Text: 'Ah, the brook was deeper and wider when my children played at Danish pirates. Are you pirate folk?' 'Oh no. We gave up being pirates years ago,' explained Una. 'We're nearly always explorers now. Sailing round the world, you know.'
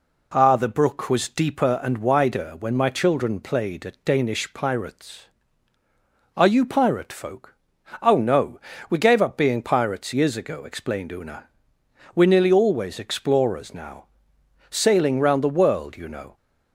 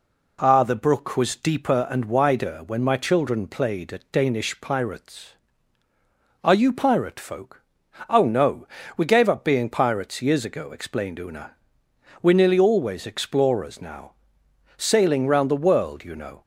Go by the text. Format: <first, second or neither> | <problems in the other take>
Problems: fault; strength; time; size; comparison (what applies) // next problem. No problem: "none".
neither | none